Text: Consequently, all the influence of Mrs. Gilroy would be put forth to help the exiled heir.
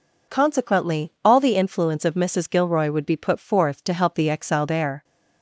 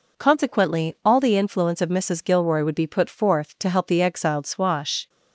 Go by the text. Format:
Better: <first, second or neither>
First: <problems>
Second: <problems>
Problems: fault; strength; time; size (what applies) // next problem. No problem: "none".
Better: first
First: none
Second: says "swash" for "heir"; at 4.4 s